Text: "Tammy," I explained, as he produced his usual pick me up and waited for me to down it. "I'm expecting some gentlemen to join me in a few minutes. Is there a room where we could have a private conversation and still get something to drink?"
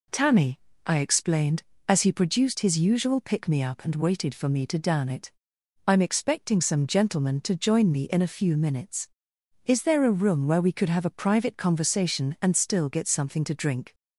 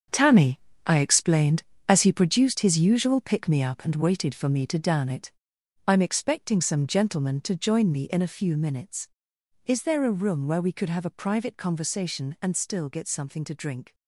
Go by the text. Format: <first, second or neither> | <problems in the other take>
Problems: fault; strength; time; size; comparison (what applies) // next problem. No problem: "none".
first | gets quieter; strong; throughout; 11 dB